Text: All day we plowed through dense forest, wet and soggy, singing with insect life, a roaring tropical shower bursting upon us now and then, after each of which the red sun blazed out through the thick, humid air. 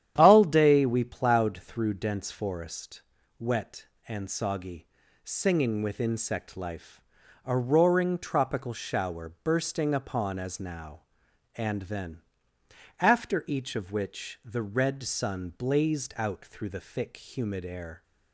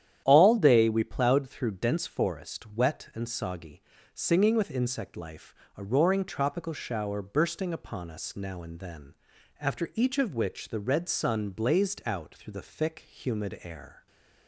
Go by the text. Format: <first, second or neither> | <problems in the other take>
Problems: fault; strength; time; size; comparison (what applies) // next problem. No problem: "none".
second | starts louder than the rest; strong; until 1.1 s; 10 dB; strong in the second // says "as" for "us"; at 10.3 s